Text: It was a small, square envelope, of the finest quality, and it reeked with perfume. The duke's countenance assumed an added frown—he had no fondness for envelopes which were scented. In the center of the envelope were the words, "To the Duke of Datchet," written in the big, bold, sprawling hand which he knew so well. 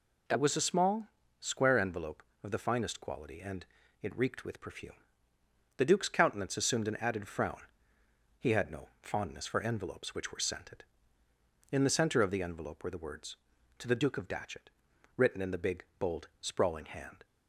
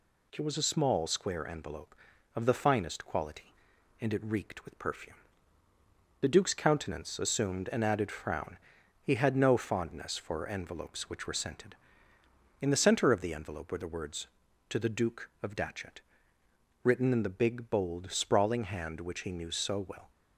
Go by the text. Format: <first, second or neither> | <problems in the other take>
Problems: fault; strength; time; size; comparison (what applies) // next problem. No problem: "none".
second | pauses between "and" and "it"; at 3.6 s; 0.38 s long // stops before "which he knew so well"; at 17.2 s